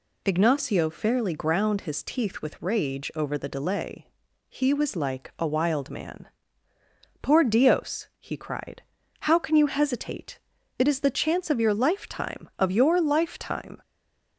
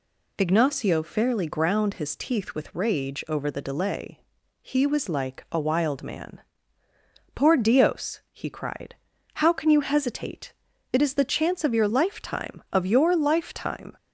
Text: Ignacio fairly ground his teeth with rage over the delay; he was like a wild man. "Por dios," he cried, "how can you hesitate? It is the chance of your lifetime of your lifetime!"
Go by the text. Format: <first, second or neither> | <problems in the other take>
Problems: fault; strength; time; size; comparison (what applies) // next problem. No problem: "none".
second | stays silent after the last word; slight; from 13.8 s on; 0.5 s long